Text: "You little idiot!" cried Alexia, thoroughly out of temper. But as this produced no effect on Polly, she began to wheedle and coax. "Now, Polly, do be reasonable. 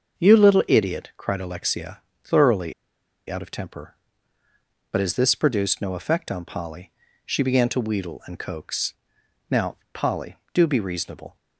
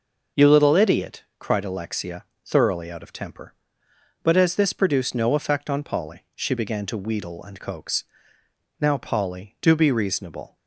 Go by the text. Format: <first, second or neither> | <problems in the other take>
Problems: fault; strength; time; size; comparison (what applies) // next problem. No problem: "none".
second | starts louder than the rest; until 1.2 s; 6.5 dB // pauses between "thoroughly" and "out"; noticeable; at 2.7 s; 0.56 s long